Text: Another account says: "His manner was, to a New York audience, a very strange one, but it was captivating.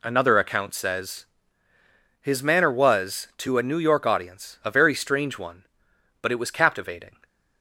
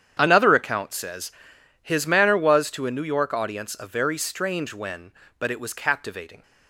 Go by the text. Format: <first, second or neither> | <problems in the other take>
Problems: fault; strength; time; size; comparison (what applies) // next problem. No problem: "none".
first | starts louder than the rest; strong; until 1.2 s; 9 dB // says "when" for "one"; at 4.7 s